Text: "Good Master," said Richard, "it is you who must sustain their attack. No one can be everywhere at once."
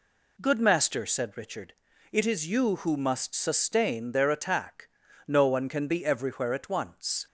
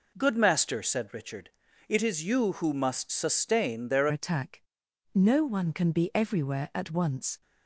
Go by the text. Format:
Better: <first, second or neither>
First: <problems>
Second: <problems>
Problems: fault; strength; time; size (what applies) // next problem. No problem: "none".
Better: first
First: none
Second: changes voice at "attack"; from 4.1 s on; 3.3 s long